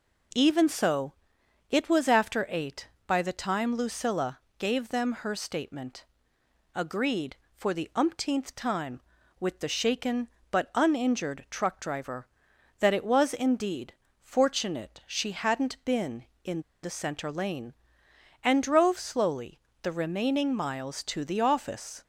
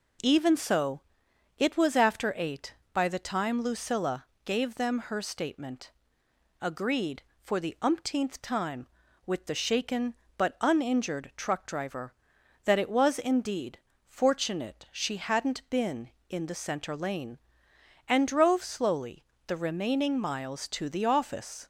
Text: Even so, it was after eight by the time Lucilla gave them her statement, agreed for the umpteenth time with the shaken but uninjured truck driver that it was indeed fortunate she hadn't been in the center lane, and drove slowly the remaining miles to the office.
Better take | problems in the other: second | pauses between "Lucilla" and "gave"; slight; at 4.3 s; 0.20 s long; slight in the second // pauses between "indeed" and "fortunate"; slight; at 13.9 s; 0.32 s long; slight in the second // pauses between "in" and "the"; slight; at 16.6 s; 0.21 s long // pauses between "slowly" and "the"; slight; at 19.5 s; 0.22 s long; slight in the second

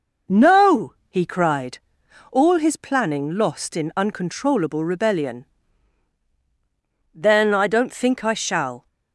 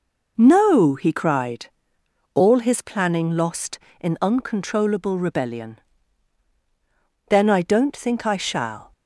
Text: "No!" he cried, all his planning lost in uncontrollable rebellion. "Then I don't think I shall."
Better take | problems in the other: neither | none

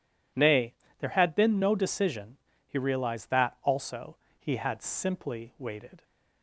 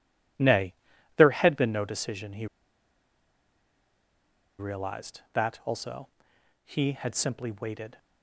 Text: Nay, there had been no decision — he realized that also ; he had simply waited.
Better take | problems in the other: first | pauses between "he" and "realized"; strong; at 2.4 s; 2.1 s long

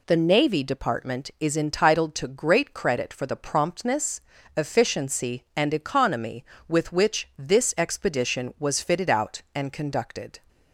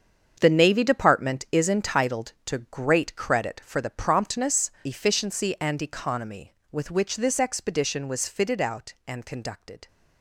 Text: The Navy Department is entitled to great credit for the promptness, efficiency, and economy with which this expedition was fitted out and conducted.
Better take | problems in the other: first | gets quieter; strong; throughout; 12.5 dB

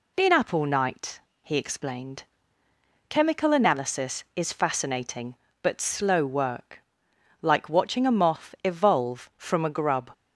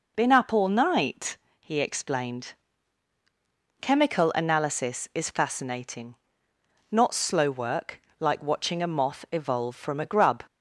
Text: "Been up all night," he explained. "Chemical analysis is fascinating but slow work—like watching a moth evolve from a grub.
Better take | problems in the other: first | says "not" for "but"; at 6.9 s

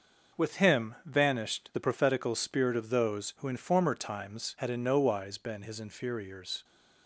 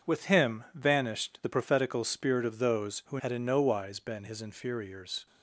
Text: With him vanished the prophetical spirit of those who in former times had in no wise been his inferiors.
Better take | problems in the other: first | starts louder than the rest; until 1.1 s; 7 dB; noticeable in the first // skips "in former times"; at 3.1 s

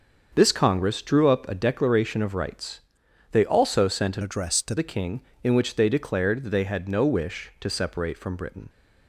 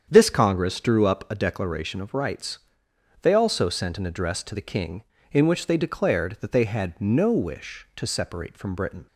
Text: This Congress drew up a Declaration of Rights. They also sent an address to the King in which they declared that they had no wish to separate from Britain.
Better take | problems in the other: second | starts louder than the rest; until 1.3 s; 6.5 dB; strong in the second // changes voice from "address" to "to"; from 4.2 to 4.7 s; 0.5 s long

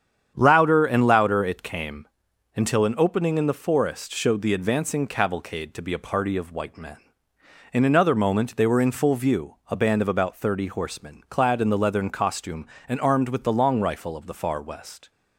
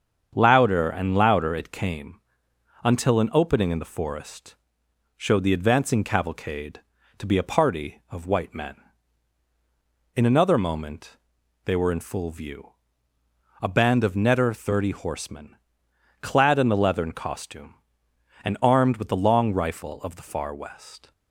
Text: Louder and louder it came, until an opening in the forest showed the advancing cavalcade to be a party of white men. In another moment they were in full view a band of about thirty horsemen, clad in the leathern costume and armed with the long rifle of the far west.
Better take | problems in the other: first | starts louder than the rest; strong; until 1.3 s; 7.5 dB; strong in the first // pauses between "forest" and "showed"; noticeable; at 4.5 s; 0.60 s long // pauses between "moment" and "they"; noticeable; at 11.1 s; 0.48 s long // pauses between "view" and "a"; noticeable; at 12.7 s; 0.90 s long // says "netter" for "about"; at 14.1 s

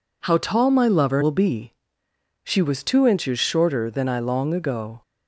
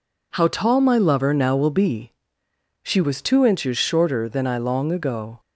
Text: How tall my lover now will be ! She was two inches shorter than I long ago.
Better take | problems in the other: second | skips "now"; at 1.2 s

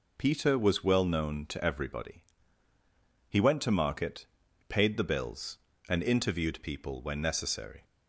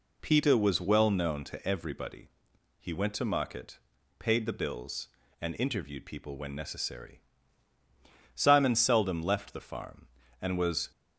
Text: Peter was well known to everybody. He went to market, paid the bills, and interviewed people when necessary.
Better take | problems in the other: first | goes on to say "Simon seldom left the farm and was"; strong; from 8.3 s on; 2.5 s long

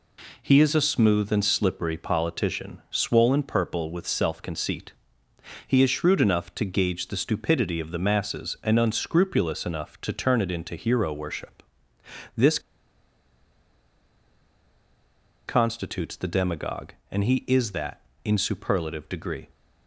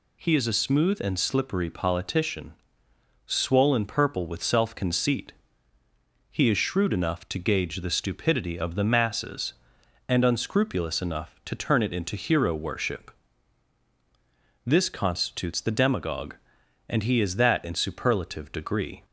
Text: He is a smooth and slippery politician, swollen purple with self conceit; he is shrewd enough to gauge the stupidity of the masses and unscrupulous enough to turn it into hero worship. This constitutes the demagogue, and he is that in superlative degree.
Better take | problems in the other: second | pauses between "This" and "constitutes"; strong; at 12.5 s; 2.8 s long

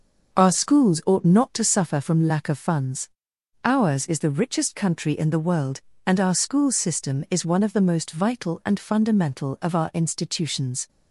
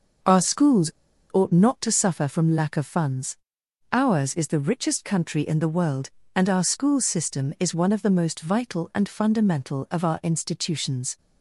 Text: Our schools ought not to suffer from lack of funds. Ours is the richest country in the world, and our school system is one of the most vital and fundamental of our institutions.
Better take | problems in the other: first | pauses between "schools" and "ought"; at 0.9 s; 0.41 s long

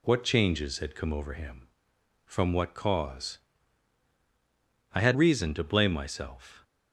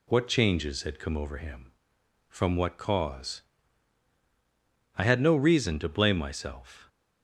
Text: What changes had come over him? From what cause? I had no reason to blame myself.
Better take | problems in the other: second | skips "no"; at 5.1 s

